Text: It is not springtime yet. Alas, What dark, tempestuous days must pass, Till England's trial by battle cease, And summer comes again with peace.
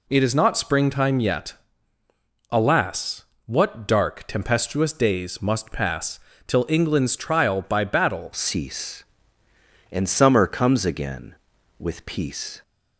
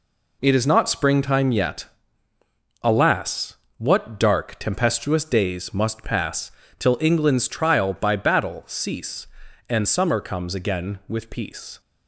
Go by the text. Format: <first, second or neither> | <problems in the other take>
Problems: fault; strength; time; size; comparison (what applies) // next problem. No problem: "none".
second | changes voice at "cease"; from 8.3 s on; 4.3 s long